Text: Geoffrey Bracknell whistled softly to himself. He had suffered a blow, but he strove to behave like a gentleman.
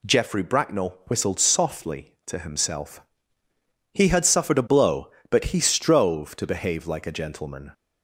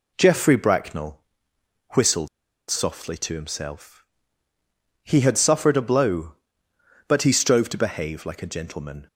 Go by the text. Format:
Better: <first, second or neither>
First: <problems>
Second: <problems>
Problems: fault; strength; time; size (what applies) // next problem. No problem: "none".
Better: first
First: none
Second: pauses between "Bracknell" and "whistled"; noticeable; at 1.1 s; 0.76 s long // pauses between "whistled" and "softly"; at 2.2 s; 0.40 s long